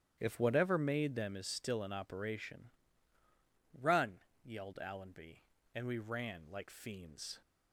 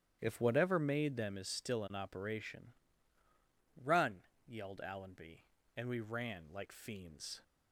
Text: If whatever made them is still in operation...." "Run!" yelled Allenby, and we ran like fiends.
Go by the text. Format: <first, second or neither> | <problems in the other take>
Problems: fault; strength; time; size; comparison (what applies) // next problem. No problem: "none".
neither | starts louder than the rest; strong; the same in both